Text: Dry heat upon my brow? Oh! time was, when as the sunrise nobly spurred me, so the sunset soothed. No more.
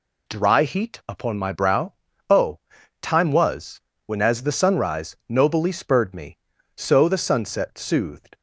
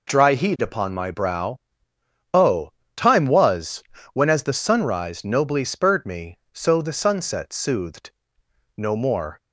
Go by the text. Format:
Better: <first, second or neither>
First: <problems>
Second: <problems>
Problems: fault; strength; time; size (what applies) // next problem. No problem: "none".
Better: second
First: stops before "No more"; at 8.3 s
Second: none